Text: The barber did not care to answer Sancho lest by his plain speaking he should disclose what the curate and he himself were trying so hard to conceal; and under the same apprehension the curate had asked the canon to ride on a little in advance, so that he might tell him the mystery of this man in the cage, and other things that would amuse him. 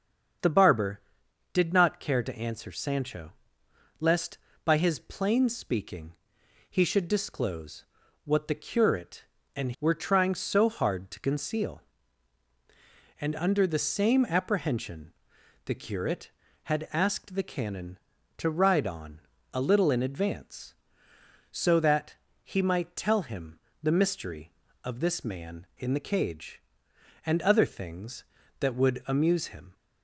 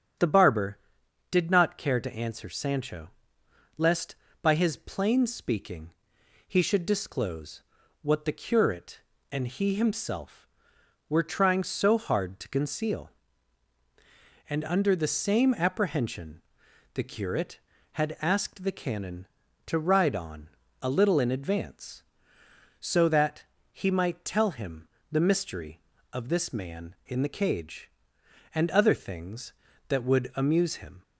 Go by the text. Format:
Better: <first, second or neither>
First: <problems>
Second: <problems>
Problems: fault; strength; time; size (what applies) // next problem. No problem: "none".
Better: second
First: starts louder than the rest; strong; until 1.9 s; 7 dB // pauses between "Sancho" and "lest"; noticeable; at 3.3 s; 0.70 s long // pauses between "speaking" and "he"; noticeable; at 6.1 s; 0.56 s long // pauses between "disclose" and "what"; at 7.8 s; 0.40 s long // skips "he himself"; at 9.7 s // pauses between "apprehension" and "the"; noticeable; at 15.1 s; 0.54 s long // pauses between "on" and "a"; slight; at 19.1 s; 0.34 s long // pauses between "that" and "he"; slight; at 22.1 s; 0.28 s long // pauses between "him" and "the"; slight; at 23.5 s; 0.24 s long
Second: starts louder than the rest; strong; until 1.7 s; 8 dB // pauses between "Sancho" and "lest"; noticeable; at 3.0 s; 0.70 s long // pauses between "speaking" and "he"; noticeable; at 5.9 s; 0.56 s long // pauses between "disclose" and "what"; at 7.6 s; 0.40 s long // pauses between "apprehension" and "the"; noticeable; at 16.3 s; 0.54 s long // pauses between "on" and "a"; slight; at 20.4 s; 0.34 s long // pauses between "that" and "he"; slight; at 23.4 s; 0.28 s long // pauses between "him" and "the"; slight; at 24.8 s; 0.24 s long